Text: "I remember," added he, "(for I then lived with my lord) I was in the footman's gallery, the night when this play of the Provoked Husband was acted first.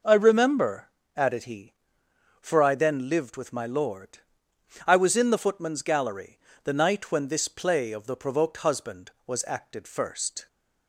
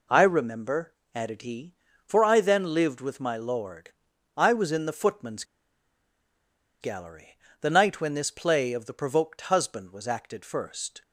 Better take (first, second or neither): first